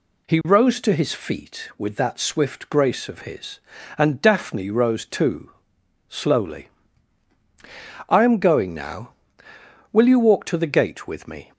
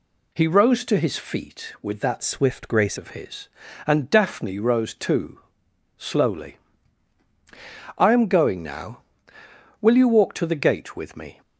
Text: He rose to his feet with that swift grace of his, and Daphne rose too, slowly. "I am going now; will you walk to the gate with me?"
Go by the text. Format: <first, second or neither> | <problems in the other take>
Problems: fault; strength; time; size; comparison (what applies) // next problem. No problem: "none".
first | changes voice from "swift" to "grace"; from 2.2 to 2.9 s; 0.7 s long